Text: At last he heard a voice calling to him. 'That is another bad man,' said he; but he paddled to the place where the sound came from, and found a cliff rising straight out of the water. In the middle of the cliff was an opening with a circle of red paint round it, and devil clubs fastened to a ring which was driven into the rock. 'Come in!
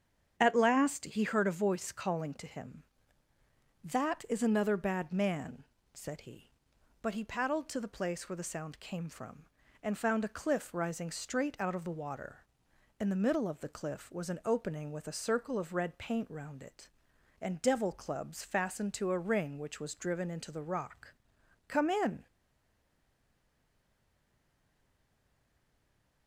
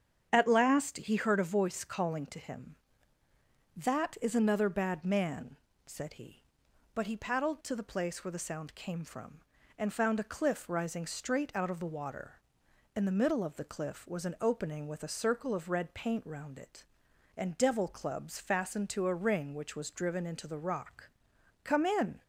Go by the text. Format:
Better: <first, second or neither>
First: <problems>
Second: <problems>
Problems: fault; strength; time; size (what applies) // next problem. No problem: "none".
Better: second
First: starts louder than the rest; strong; until 1.3 s; 8 dB // stays silent after the last word; strong; from 22.2 s on; 4.0 s long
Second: starts louder than the rest; strong; until 1.3 s; 8 dB